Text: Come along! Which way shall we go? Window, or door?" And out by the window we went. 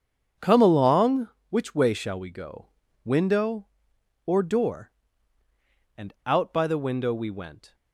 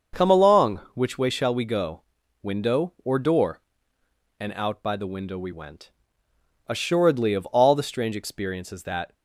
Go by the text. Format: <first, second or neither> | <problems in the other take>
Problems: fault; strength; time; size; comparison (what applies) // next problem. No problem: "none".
first | starts louder than the rest; until 1.3 s; 6.5 dB; strong in the first // goes on to say "Assuredly of all the strange experiences that"; strong; from 6.6 s on; 2.4 s long